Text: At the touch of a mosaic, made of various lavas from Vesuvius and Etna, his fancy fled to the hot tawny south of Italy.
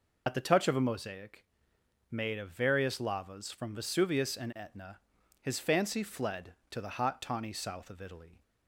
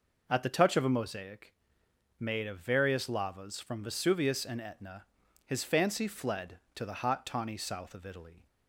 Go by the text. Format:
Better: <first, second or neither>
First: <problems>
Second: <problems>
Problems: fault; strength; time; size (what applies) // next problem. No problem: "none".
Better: second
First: loses the start of "At"; at 0.2 s; 55 ms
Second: none